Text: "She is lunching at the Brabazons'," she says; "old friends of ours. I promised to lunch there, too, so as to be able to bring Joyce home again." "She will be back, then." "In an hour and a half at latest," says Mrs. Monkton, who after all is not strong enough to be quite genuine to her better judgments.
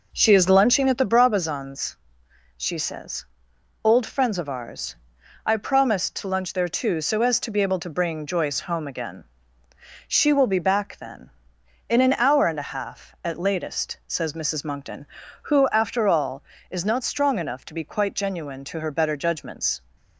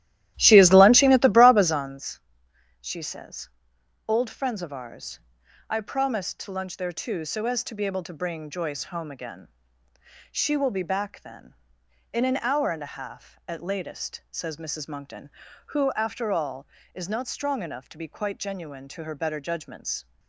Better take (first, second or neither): first